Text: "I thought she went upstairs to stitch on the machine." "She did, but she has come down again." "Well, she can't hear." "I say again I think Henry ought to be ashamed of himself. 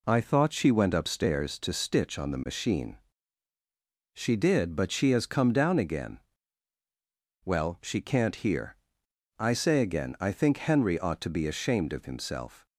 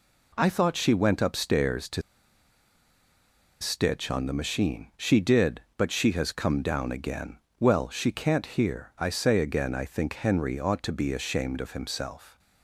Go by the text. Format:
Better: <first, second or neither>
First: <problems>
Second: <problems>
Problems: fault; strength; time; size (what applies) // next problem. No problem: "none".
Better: first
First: none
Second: pauses between "to" and "stitch"; strong; at 2.0 s; 1.5 s long